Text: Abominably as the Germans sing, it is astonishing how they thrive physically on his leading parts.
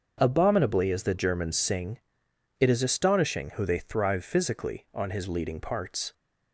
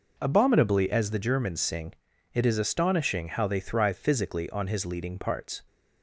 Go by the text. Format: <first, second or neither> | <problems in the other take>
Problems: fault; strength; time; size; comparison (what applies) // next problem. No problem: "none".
second | starts louder than the rest; until 1.2 s; 6.5 dB // says "who" for "how"; at 3.5 s